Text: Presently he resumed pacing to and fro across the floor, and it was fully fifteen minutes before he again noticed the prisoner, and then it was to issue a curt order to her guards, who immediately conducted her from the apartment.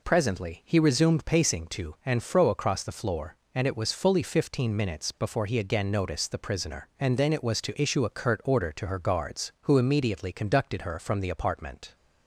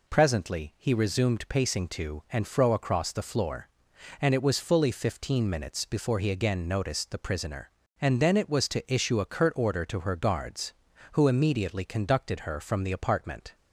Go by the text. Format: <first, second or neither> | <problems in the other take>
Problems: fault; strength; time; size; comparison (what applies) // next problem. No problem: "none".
neither | none